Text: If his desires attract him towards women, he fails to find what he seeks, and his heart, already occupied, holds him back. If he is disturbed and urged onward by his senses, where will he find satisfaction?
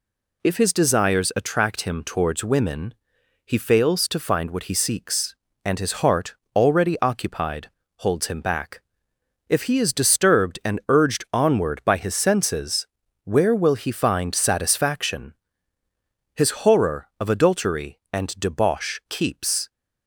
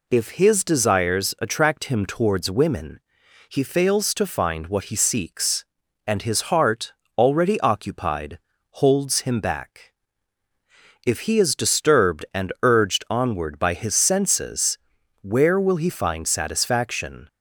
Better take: second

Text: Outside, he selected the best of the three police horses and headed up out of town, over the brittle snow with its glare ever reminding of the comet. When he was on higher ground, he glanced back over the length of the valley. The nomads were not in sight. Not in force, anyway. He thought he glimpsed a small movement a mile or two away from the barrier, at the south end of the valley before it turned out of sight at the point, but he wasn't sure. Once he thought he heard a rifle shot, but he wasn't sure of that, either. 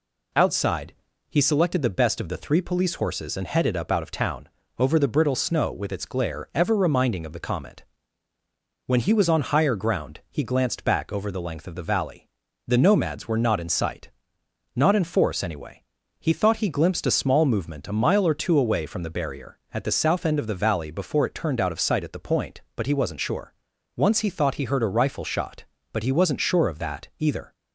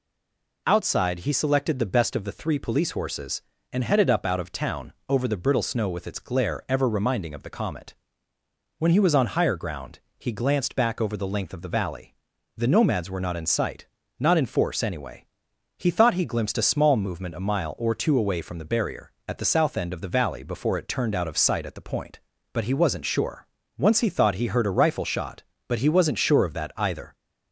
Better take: first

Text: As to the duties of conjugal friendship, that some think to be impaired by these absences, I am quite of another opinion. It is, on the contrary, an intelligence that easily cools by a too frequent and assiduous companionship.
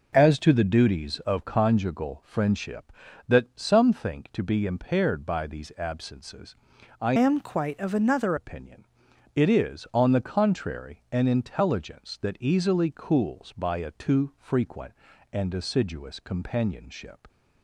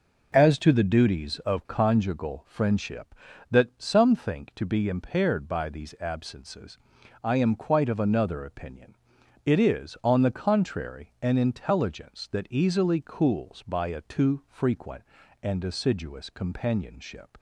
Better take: second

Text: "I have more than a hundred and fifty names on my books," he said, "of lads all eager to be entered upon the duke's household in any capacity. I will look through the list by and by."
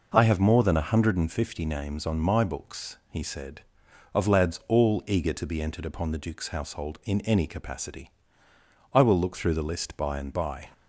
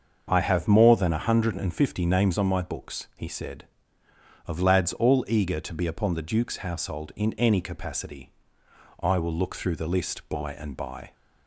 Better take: first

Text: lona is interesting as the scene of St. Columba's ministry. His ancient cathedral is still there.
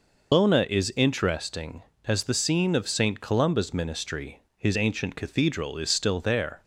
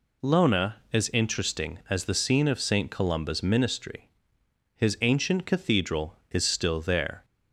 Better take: second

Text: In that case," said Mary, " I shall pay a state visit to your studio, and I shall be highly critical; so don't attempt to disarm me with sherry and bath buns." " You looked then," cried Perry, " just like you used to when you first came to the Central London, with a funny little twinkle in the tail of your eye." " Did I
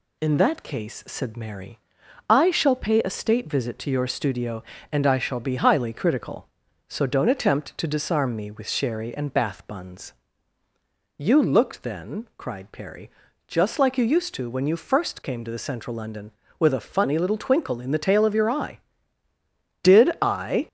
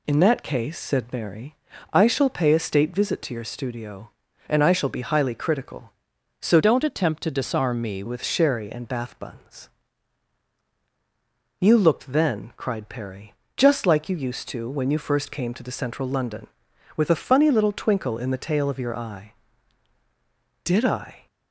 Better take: first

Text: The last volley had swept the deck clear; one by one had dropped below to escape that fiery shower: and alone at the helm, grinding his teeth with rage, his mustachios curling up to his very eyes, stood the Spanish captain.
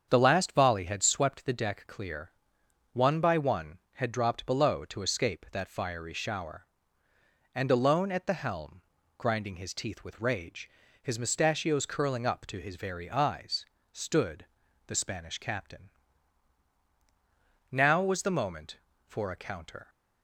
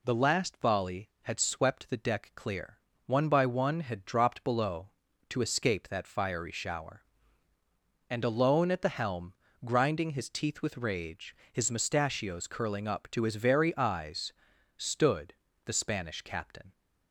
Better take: second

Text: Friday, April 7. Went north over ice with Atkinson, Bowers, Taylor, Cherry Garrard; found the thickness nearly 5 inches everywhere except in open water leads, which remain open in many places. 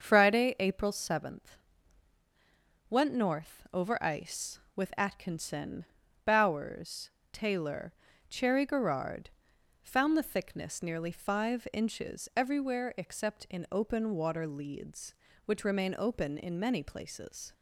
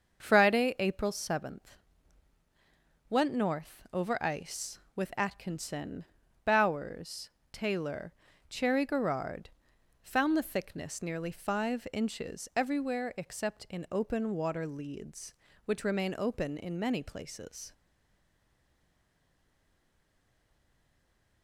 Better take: first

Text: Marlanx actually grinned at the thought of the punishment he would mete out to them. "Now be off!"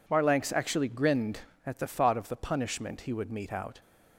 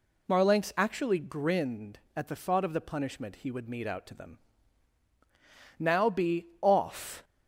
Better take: second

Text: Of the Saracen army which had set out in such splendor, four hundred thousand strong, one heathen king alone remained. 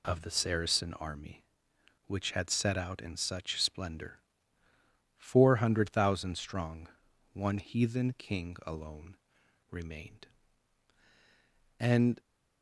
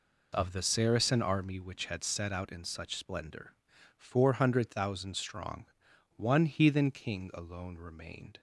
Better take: second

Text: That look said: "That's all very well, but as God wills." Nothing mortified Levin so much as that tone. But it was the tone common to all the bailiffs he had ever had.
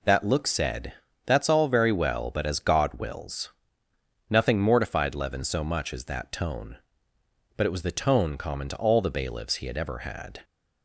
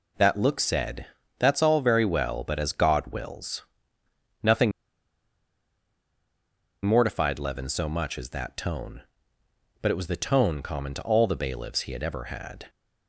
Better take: first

